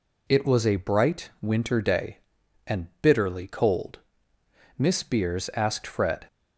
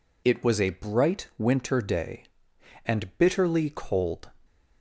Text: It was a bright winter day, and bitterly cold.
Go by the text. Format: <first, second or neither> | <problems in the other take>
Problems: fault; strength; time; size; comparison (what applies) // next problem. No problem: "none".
second | goes on to say "Miss Beers asked Fred"; from 4.7 s on; 1.5 s long